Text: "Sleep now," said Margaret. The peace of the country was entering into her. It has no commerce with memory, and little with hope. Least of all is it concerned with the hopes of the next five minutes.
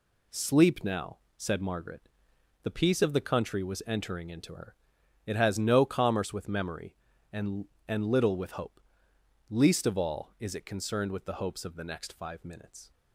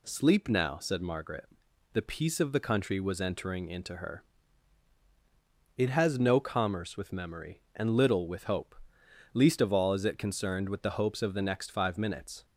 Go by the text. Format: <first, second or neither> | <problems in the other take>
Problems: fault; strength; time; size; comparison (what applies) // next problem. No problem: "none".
second | says "and" twice; at 7.8 s